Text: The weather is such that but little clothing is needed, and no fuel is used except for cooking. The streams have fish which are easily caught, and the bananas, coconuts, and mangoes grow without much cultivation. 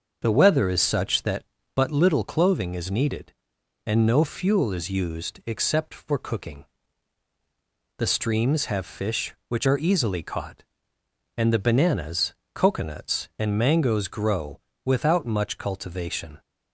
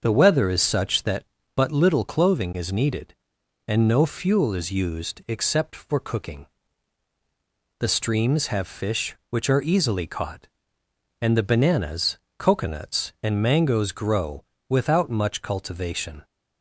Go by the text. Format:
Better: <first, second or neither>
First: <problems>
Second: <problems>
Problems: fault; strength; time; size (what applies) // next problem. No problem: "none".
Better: neither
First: starts louder than the rest; until 1.2 s; 6.5 dB // pauses between "grow" and "without"; slight; at 14.5 s; 0.26 s long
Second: starts louder than the rest; until 1.0 s; 6.5 dB // pauses between "grow" and "without"; slight; at 14.4 s; 0.26 s long